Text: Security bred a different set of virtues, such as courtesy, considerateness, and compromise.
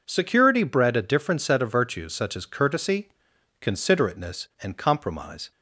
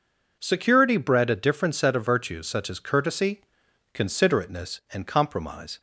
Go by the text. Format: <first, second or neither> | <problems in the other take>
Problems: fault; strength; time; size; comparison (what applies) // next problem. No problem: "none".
neither | none